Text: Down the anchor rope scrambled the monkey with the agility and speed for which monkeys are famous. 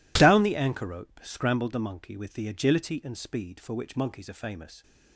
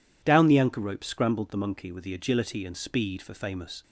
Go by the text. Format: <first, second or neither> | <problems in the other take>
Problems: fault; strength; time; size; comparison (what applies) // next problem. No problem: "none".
first | skips "which monkeys are"; at 3.3 s